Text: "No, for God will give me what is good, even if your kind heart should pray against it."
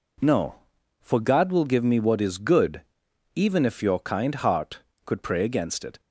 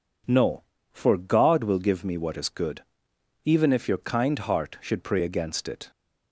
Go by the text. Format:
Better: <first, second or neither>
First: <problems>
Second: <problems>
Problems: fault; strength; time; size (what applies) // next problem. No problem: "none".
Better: second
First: says "could" for "should"; at 5.0 s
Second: none